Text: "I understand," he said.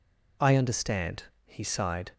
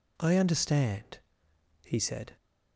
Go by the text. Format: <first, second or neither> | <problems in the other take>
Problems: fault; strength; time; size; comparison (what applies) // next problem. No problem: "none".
second | says "sighed" for "said"; at 1.6 s